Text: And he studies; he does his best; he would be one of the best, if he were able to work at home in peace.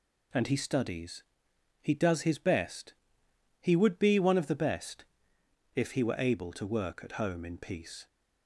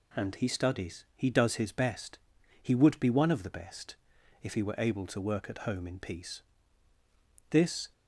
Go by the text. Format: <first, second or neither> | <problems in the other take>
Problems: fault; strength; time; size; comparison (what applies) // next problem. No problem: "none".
first | goes on to say "This"; slight; from 7.5 s on; 0.42 s long